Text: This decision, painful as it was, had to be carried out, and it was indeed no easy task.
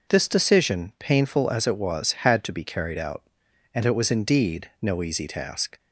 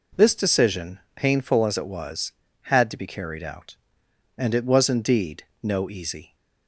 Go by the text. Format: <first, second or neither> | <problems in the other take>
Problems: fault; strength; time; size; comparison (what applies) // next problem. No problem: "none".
first | pauses between "indeed" and "no"; slight; at 5.4 s; 0.18 s long // stops before "task"; at 6.3 s